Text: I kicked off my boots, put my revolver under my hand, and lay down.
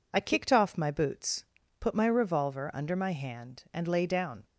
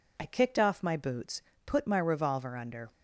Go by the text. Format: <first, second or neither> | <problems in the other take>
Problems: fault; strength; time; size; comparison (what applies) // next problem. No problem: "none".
first | stops before "my hand and lay down"; at 2.9 s